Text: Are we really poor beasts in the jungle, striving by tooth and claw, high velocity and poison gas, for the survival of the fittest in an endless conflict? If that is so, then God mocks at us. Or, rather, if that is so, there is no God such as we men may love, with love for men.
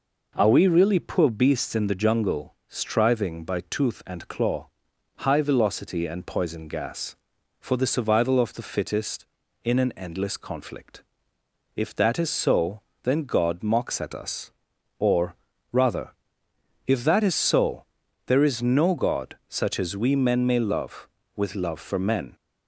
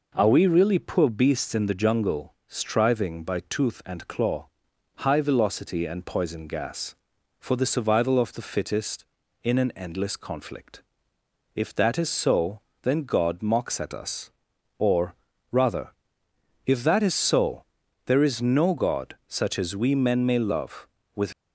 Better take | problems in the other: first | stops before "love for men"; at 21.3 s

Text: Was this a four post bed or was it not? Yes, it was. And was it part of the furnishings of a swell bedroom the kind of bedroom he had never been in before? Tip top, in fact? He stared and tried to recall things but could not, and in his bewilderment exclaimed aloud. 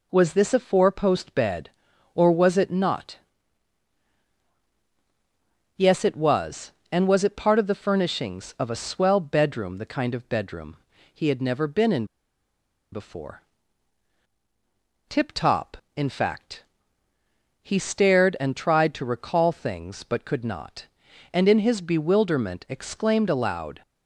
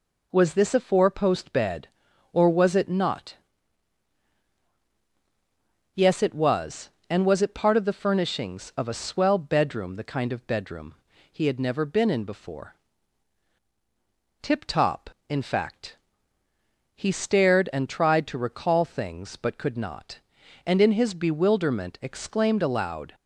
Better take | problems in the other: second | pauses between "bedroom" and "he"; at 10.7 s; 0.38 s long; also in the second // pauses between "in" and "before"; noticeable; at 12.0 s; 0.87 s long

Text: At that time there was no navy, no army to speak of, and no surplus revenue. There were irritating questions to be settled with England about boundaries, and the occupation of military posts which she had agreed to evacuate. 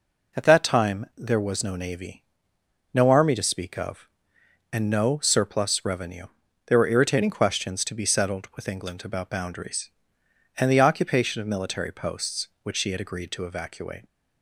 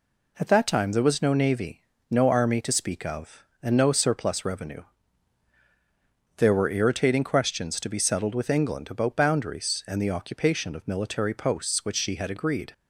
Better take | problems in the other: first | stops before "to evacuate"; at 12.7 s

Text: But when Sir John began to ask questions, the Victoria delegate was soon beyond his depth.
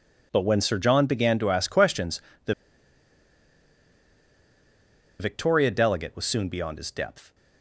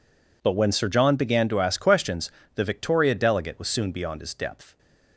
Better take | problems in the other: second | pauses between "the" and "Victoria"; strong; at 2.5 s; 2.6 s long

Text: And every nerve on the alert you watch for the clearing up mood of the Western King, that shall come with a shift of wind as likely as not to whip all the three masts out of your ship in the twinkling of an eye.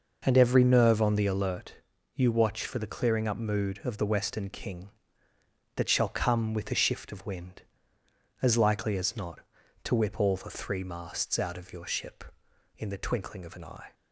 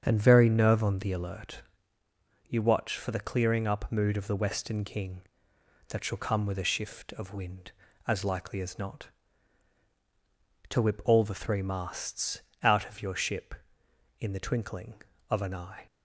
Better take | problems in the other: first | starts louder than the rest; strong; until 1.0 s; 7.5 dB // says "very" for "every"; at 0.1 s // pauses between "alert" and "you"; noticeable; at 1.6 s; 0.84 s long; also in the first // pauses between "masts" and "out"; slight; at 12.4 s; 0.20 s long

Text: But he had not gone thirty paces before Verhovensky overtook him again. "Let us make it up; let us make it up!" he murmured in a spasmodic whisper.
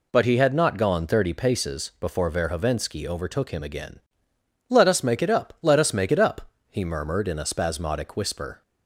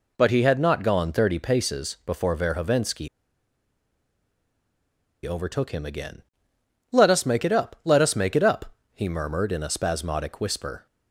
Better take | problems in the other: first | pauses between "Verhovensky" and "overtook"; strong; at 3.0 s; 2.1 s long

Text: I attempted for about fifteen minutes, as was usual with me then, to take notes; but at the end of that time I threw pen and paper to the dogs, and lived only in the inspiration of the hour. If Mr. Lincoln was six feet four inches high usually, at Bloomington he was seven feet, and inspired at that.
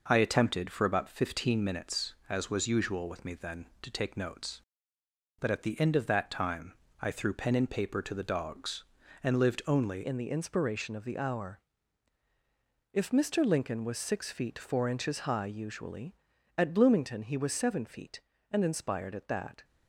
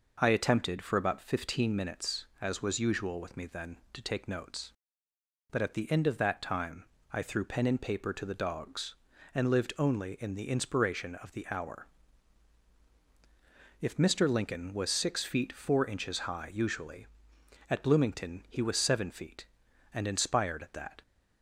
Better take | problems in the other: second | pauses between "time" and "I"; slight; at 6.7 s; 0.28 s long; slight in the second // changes voice at "in"; from 10.0 s on; 9.6 s long

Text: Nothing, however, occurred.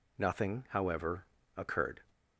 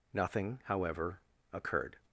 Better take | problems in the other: neither | none

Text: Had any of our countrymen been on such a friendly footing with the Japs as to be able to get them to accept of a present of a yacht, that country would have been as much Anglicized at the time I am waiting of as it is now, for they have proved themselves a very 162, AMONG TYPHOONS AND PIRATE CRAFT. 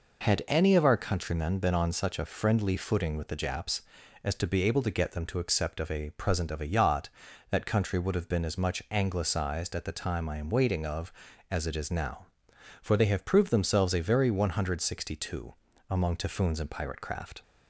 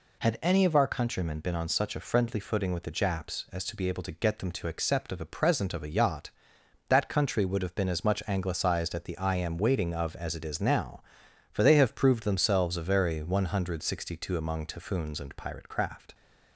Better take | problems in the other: first | skips "time"; at 9.1 s

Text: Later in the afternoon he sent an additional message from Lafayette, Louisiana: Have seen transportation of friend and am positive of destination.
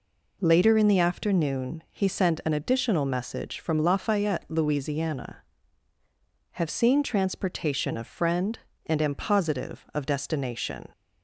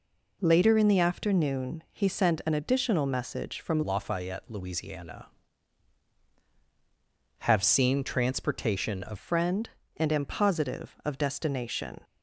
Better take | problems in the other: first | changes voice from "Lafayette" to "of"; from 3.8 to 9.1 s; 5.3 s long

